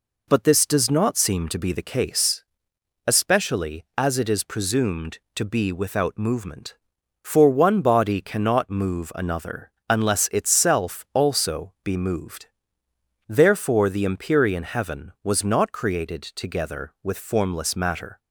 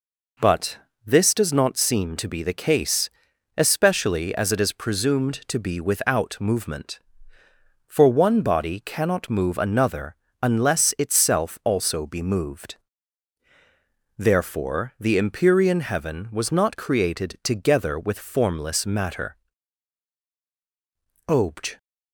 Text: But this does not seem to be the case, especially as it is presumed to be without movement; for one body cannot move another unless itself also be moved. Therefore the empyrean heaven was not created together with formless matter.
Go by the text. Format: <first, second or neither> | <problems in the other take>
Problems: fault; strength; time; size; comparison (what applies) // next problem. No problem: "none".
first | pauses between "But" and "this"; slight; at 0.7 s; 0.28 s long // pauses between "another" and "unless"; slight; at 10.1 s; 0.28 s long; slight in the first // goes on to say "Obj"; from 21.2 s on; 0.50 s long